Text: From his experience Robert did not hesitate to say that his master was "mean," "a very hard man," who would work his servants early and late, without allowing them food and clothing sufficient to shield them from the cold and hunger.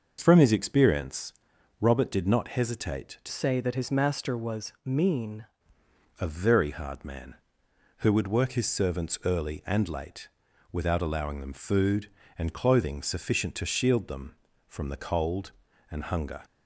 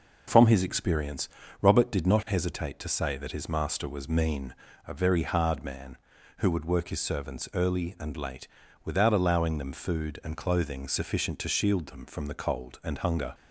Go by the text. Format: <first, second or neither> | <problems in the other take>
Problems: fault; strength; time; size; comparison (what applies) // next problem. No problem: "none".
second | starts louder than the rest; noticeable; until 1.2 s; 6 dB // pauses between "experience" and "Robert"; noticeable; at 1.3 s; 0.48 s long; slight in the second // changes voice from "say" to "mean"; from 3.2 to 5.4 s; 2.2 s long